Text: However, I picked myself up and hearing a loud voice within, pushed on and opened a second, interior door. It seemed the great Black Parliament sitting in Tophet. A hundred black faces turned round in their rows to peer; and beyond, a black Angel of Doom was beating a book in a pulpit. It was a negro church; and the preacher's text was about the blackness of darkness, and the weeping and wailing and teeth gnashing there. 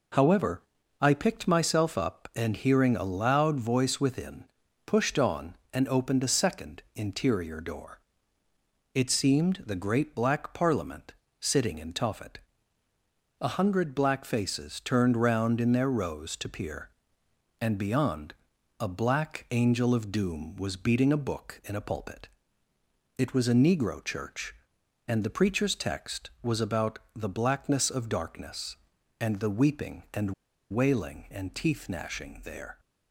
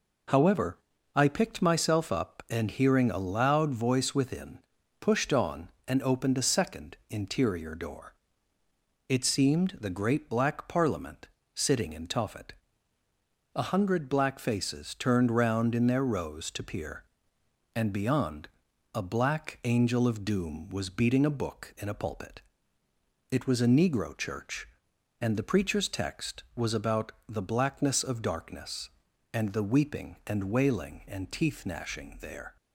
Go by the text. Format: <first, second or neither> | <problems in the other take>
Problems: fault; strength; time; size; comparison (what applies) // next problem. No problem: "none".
second | pauses between "Parliament" and "sitting"; slight; at 11.1 s; 0.24 s long; slight in the second // pauses between "about" and "the"; slight; at 26.9 s; 0.16 s long; slight in the second // pauses between "and" and "wailing"; at 30.3 s; 0.39 s long